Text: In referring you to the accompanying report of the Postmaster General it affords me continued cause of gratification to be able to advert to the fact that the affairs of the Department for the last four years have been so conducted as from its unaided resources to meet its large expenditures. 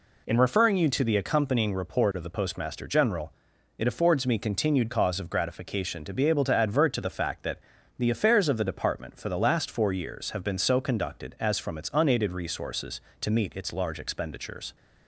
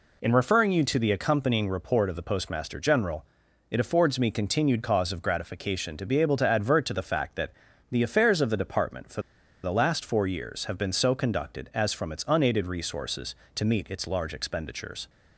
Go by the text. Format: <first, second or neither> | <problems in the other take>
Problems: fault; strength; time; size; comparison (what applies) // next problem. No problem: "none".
first | pauses between "General" and "it"; at 3.2 s; 0.44 s long; also in the first // pauses between "that" and "the"; at 7.4 s; 0.40 s long; also in the first // pauses between "for" and "the"; at 9.2 s; 0.41 s long